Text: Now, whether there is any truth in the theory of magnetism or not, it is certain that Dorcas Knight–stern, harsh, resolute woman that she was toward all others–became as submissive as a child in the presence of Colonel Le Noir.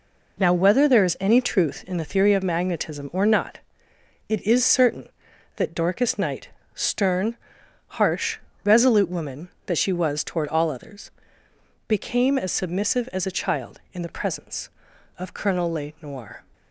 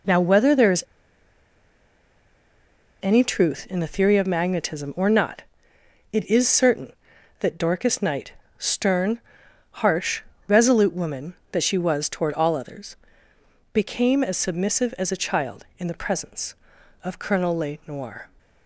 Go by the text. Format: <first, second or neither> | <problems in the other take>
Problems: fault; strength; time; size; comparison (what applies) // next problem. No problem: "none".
first | pauses between "is" and "any"; strong; at 0.8 s; 2.1 s long